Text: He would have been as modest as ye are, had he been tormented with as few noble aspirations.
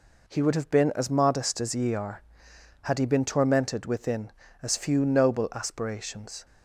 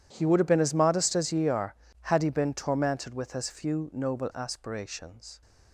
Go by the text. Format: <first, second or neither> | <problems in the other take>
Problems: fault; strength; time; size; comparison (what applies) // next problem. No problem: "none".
second | says "within" for "with"; at 3.8 s